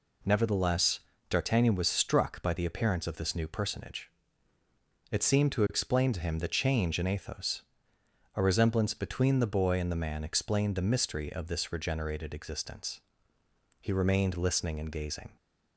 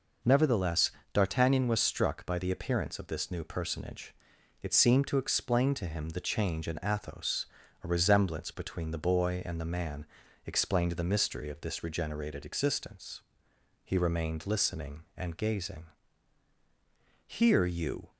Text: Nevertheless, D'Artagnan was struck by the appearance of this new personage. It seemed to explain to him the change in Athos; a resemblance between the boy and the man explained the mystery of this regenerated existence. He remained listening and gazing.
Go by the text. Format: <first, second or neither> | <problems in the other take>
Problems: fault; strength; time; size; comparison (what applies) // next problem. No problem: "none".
first | pauses between "man" and "explained"; at 10.0 s; 0.40 s long // goes on to say "Here you"; noticeable; from 17.2 s on; 0.84 s long